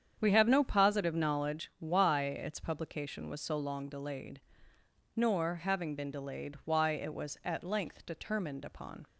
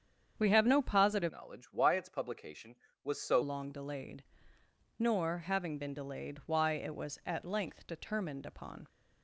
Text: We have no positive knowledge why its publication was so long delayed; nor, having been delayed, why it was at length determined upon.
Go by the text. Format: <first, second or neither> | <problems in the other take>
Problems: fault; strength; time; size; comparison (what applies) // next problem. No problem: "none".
first | starts louder than the rest; strong; until 1.3 s; 8 dB; strong in the first // changes voice from "knowledge" to "so"; from 1.2 to 3.4 s; 2.2 s long